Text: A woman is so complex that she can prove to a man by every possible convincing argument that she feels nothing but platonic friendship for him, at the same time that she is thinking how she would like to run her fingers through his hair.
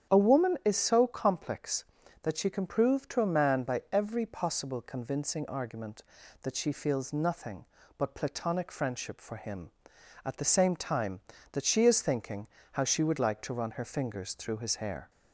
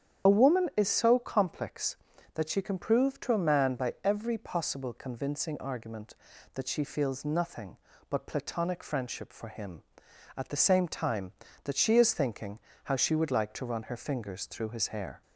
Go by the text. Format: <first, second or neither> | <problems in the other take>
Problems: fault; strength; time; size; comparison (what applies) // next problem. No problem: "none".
first | loses the start of "A"; at 0.2 s; 35 ms // starts louder than the rest; strong; until 1.3 s; 8.5 dB; strong in the first // pauses between "thinking" and "how"; slight; at 12.5 s; 0.24 s long; slight in the first